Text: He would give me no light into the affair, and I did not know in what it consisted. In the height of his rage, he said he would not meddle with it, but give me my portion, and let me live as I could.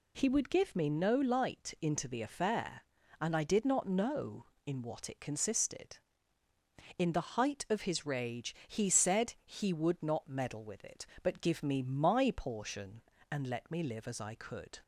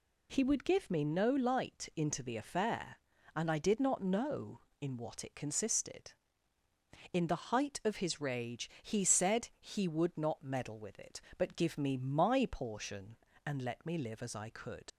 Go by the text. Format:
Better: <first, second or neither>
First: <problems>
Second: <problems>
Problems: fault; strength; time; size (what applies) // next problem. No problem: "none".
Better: first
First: none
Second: leaves "could" unfinished; at 14.9 s; 65 ms